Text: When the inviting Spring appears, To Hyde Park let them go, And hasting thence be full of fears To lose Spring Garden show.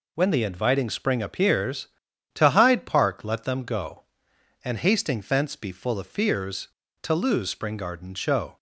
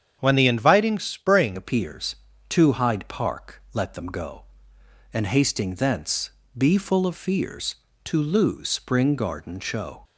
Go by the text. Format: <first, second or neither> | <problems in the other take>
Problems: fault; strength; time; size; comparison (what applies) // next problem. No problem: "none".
first | starts louder than the rest; strong; until 1.2 s; 8 dB // changes voice at "appears"; from 1.5 s on; 8.5 s long // pauses between "thence" and "be"; slight; at 6.2 s; 0.26 s long